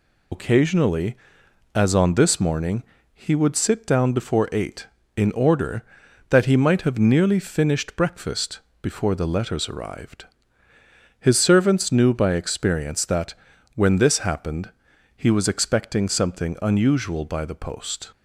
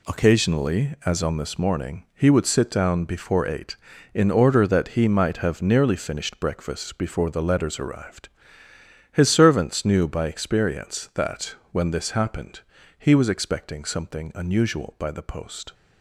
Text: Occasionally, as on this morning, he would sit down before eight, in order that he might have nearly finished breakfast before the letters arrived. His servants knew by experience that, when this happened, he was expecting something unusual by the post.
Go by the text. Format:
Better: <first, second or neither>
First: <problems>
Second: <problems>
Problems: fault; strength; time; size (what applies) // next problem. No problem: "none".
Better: second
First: loses the start of "Occasionally"; at 0.3 s; 70 ms // pauses between "breakfast" and "before"; slight; at 8.5 s; 0.24 s long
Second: none